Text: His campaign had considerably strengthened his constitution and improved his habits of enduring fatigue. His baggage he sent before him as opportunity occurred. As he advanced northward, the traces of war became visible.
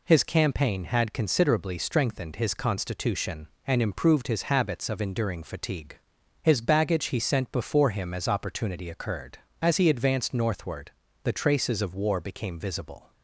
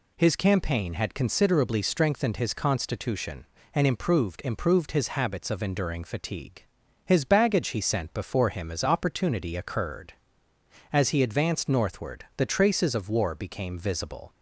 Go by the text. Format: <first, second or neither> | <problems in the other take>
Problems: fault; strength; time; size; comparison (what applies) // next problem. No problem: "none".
first | says "improved" twice; at 4.4 s